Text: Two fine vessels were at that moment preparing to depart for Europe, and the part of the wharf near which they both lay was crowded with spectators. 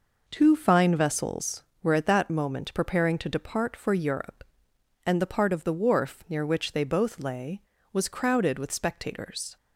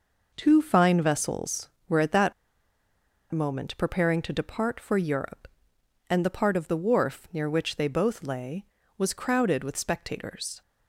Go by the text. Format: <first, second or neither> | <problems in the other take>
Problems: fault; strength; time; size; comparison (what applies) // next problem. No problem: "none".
first | pauses between "that" and "moment"; at 2.3 s; 0.98 s long